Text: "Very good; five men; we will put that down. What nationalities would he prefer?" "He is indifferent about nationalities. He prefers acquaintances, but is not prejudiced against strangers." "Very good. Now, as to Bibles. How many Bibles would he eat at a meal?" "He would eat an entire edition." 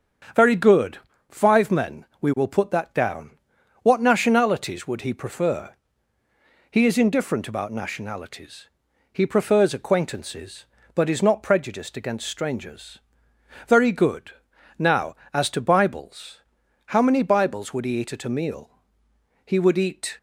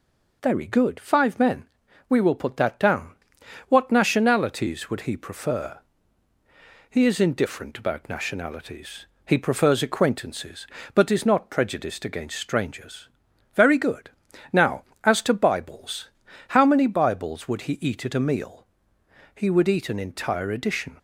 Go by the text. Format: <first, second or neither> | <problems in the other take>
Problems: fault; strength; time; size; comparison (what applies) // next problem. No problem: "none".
second | starts louder than the rest; strong; until 1.6 s; 7.5 dB // stops before "an entire edition"; at 20.1 s